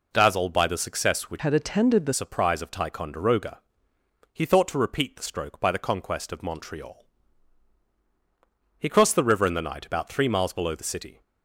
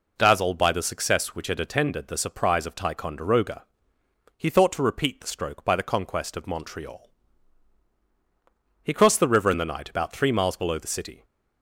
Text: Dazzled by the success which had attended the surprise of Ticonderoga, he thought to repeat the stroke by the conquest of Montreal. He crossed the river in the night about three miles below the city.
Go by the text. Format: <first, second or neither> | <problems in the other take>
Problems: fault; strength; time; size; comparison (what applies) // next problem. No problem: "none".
second | changes voice from "had" to "the"; from 1.3 to 2.1 s; 0.8 s long